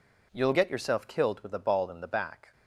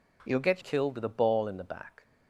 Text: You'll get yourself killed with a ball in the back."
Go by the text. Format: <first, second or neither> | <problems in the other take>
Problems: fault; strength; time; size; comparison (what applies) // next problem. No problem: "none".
first | skips "yourself"; at 0.6 s